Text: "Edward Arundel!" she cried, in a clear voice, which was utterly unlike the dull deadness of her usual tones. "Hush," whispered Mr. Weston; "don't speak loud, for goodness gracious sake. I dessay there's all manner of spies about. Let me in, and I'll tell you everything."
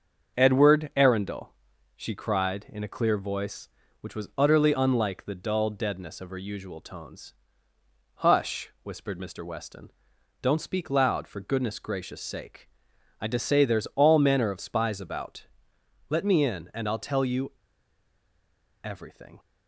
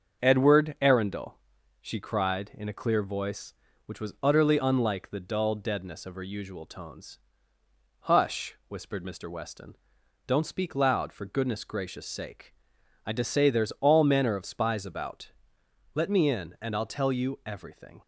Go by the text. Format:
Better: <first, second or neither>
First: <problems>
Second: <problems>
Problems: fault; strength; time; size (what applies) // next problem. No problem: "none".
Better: second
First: starts louder than the rest; until 1.4 s; 6.5 dB // pauses between "you" and "everything"; strong; at 17.5 s; 1.3 s long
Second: starts louder than the rest; until 1.2 s; 6.5 dB